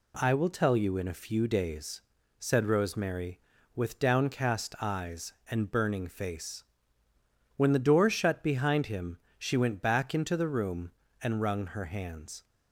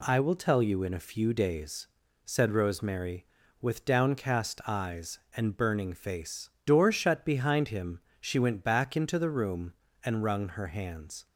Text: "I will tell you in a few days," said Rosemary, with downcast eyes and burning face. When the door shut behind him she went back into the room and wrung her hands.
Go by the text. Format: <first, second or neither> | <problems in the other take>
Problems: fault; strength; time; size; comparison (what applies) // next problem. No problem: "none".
first | skips "When the"; at 6.5 s // pauses between "him" and "she"; slight; at 7.9 s; 0.22 s long; slight in the first